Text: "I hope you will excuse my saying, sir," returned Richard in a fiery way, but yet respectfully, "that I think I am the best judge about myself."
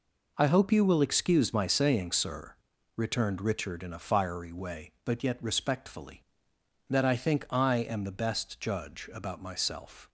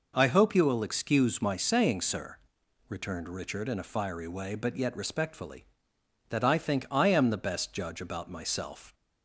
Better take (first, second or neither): neither